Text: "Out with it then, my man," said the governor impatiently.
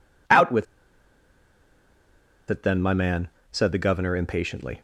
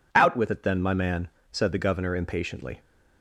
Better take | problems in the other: second | pauses between "with" and "it"; strong; at 0.6 s; 1.8 s long

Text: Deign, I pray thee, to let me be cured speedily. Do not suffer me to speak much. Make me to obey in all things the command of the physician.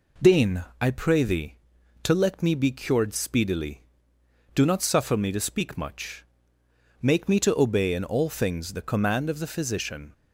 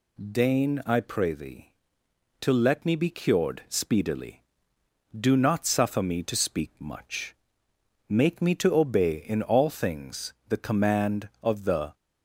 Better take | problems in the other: first | stops before "physician"; at 11.9 s

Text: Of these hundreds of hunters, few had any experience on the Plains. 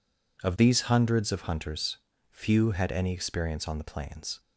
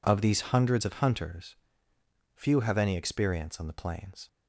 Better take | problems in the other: first | says "have" for "had"; at 2.5 s

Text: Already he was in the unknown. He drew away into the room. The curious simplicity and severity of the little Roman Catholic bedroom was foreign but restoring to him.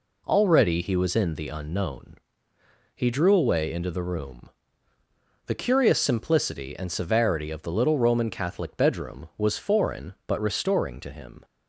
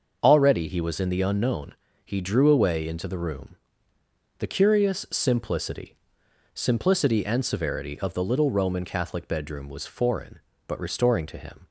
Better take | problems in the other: first | starts louder than the rest; until 1.2 s; 6 dB // says "simplicity" twice; at 6.5 s

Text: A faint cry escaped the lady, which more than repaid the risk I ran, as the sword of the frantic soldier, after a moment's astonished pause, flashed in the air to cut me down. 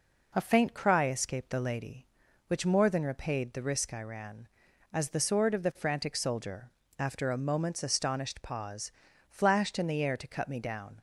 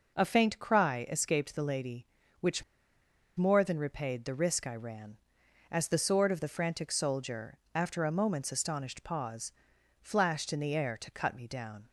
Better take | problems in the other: first | pauses between "which" and "more"; noticeable; at 2.6 s; 0.75 s long

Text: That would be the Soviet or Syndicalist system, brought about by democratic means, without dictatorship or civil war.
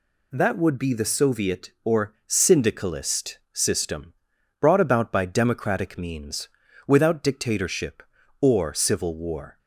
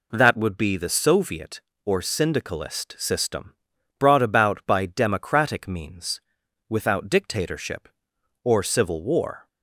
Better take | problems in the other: neither | none

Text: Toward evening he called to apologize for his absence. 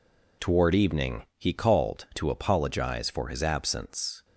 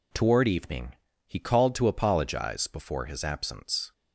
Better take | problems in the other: first | pauses between "evening" and "he"; slight; at 0.9 s; 0.32 s long; slight in the first // says "before" for "for"; at 2.6 s

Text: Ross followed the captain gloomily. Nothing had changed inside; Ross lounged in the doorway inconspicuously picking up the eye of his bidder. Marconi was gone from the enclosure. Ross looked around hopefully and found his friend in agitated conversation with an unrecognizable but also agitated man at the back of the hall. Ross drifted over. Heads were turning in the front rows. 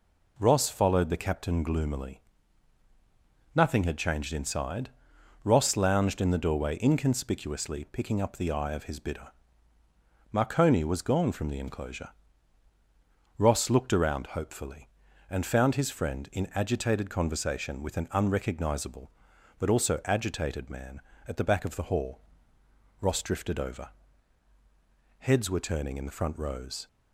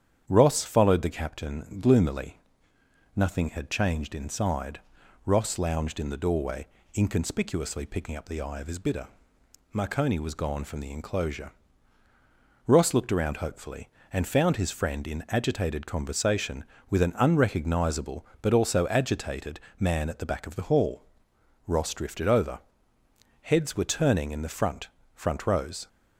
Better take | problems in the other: first | starts louder than the rest; strong; until 1.2 s; 9 dB // pauses between "doorway" and "inconspicuously"; slight; at 6.6 s; 0.26 s long // pauses between "agitated" and "man"; slight; at 19.5 s; 0.22 s long // says "front" twice; at 25.1 s

